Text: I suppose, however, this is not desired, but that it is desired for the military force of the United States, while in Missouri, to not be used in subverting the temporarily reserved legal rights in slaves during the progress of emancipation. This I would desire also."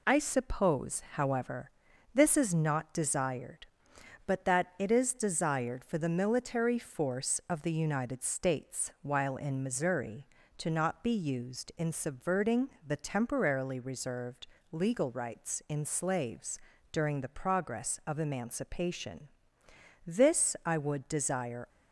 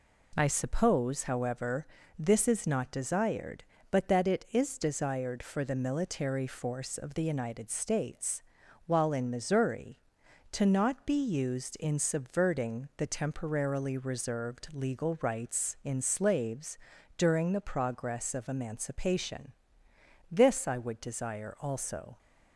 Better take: second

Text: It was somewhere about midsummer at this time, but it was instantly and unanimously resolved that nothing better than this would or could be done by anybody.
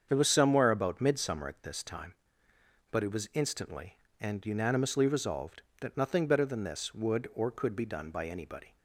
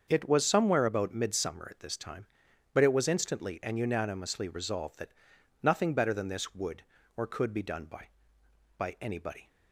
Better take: first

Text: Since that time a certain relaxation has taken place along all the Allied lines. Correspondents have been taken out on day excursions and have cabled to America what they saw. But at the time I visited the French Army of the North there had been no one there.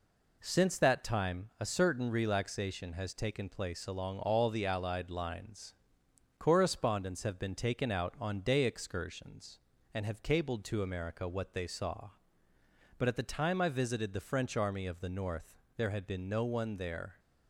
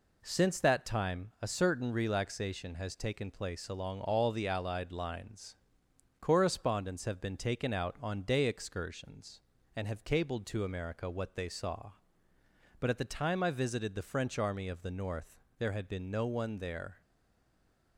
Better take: first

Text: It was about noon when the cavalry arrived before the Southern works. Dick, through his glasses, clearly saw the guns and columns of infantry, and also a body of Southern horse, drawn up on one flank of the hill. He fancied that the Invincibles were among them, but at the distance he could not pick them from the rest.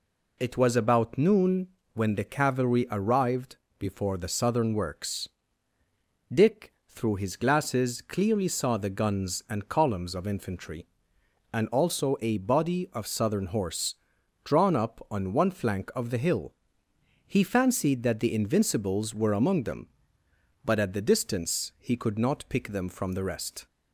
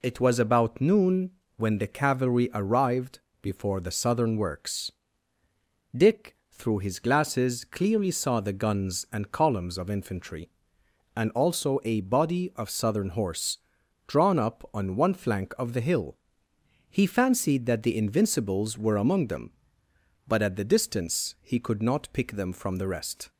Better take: neither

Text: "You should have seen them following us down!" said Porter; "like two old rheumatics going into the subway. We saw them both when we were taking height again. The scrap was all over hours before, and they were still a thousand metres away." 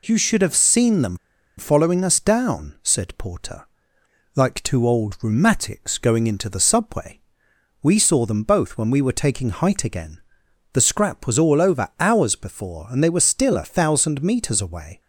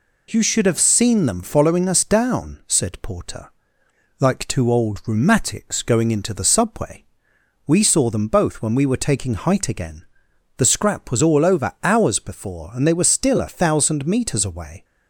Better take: second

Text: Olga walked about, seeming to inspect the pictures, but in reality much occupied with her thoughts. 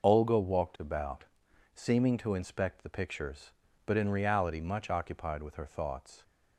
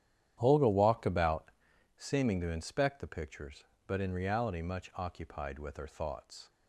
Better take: first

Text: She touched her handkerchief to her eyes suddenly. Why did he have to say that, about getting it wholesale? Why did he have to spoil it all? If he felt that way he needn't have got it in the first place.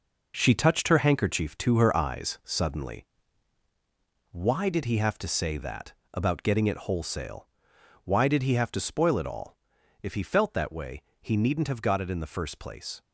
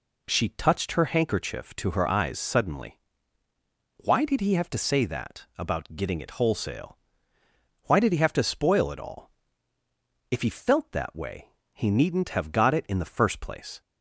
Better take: second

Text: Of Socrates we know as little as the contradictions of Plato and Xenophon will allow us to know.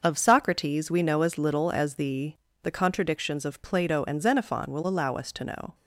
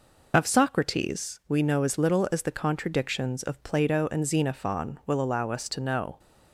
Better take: second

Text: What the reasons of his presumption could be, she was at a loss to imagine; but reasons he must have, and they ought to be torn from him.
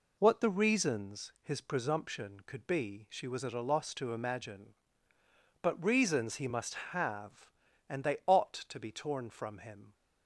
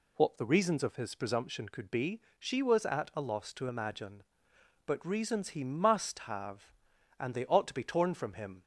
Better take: second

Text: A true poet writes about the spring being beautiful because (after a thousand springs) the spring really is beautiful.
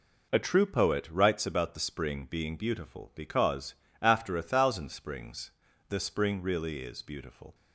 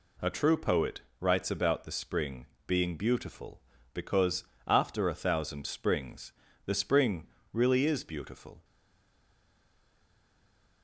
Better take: first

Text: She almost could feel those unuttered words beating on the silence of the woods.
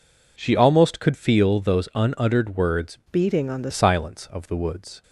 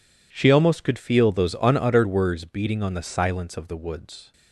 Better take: second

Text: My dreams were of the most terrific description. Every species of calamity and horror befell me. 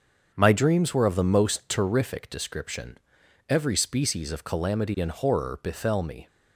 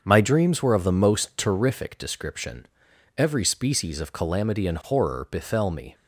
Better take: neither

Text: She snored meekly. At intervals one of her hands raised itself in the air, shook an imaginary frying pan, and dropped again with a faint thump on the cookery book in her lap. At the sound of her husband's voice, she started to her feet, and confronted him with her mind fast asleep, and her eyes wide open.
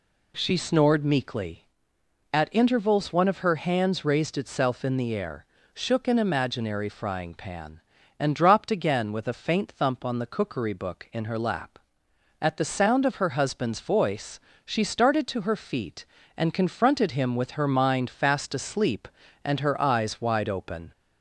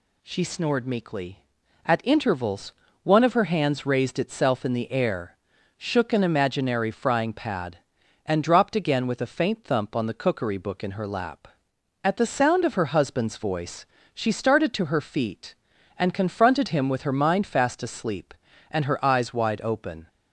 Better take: first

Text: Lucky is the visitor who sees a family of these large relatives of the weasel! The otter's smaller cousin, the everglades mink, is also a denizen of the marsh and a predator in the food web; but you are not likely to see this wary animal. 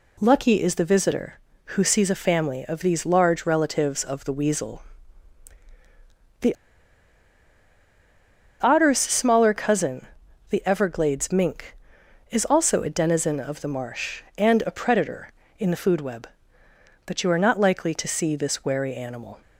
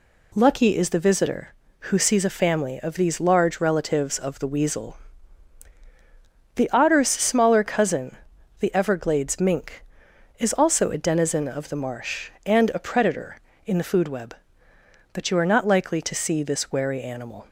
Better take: second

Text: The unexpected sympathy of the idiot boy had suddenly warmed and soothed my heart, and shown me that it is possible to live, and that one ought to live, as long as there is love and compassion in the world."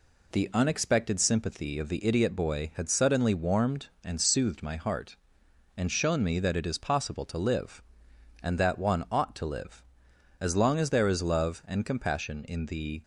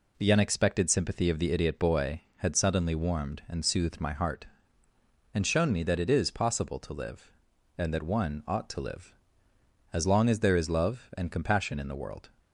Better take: second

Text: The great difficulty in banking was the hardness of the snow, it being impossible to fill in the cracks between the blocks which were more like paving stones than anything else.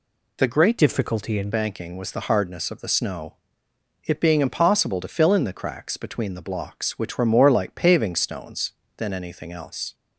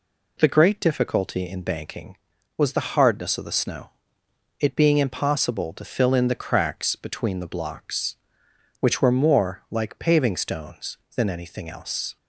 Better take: second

